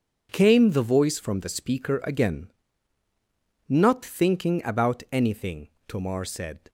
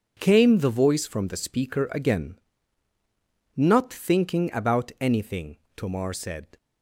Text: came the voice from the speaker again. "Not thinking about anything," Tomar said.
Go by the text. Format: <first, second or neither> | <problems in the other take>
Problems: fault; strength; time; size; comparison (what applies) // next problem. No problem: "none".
neither | none